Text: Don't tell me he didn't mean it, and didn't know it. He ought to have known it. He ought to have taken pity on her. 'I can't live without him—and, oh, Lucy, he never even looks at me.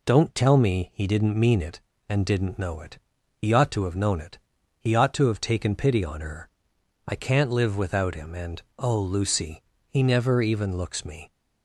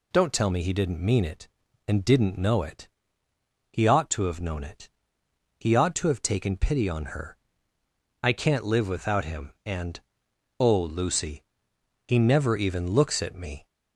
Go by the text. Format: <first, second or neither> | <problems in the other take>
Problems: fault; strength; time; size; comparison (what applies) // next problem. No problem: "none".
second | skips "at"; at 11.0 s